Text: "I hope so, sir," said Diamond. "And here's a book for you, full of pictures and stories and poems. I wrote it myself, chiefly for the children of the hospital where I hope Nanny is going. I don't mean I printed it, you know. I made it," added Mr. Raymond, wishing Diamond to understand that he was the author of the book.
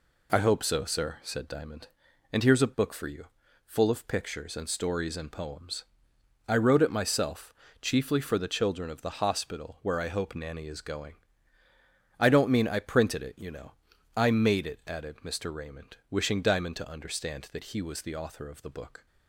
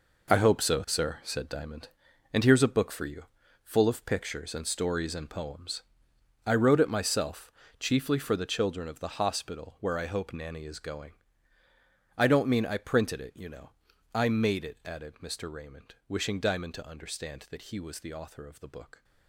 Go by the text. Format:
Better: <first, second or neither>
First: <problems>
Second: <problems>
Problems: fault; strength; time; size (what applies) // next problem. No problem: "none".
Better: first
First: none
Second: gets quieter; strong; throughout; 11.5 dB